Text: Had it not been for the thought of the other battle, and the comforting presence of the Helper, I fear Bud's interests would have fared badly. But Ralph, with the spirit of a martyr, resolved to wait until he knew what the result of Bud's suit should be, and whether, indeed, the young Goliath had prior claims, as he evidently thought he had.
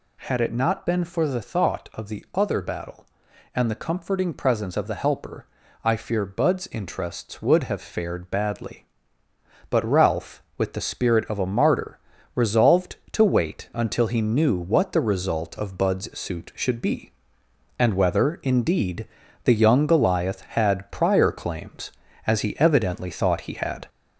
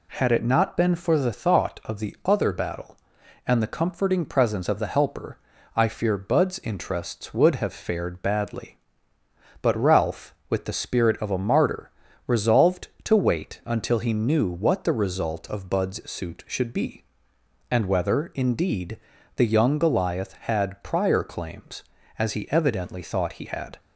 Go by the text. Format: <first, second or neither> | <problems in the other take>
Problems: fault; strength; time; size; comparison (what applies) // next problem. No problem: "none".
second | gets louder; throughout; 3.5 dB